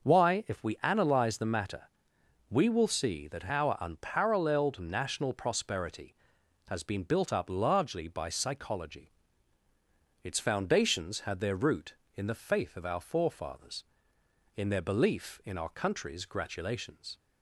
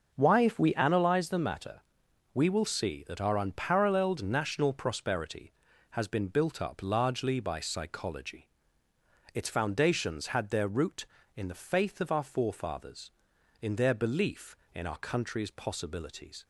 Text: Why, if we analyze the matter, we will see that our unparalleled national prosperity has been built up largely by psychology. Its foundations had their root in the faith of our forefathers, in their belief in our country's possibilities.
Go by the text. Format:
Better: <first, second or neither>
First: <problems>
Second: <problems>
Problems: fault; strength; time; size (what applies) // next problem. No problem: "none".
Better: second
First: starts louder than the rest; noticeable; until 1.1 s; 6 dB // says "gratulations" for "possibilities"; at 16.2 s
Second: starts louder than the rest; noticeable; until 1.1 s; 6 dB